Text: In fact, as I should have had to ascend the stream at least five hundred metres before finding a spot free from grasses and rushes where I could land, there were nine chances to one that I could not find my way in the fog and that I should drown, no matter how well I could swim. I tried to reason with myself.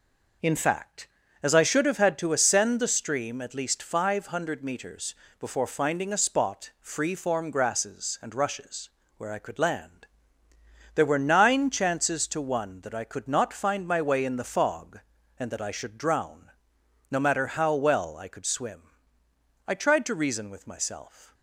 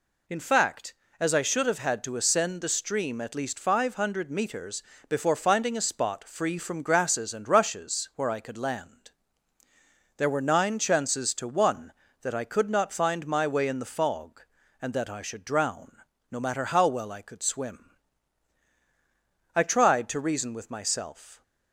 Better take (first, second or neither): second